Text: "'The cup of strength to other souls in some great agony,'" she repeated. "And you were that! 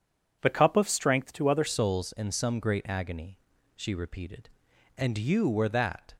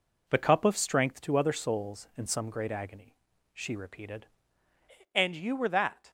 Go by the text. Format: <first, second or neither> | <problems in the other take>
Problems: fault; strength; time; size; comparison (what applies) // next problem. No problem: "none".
second | changes voice at "souls"; from 1.6 s on; 4.5 s long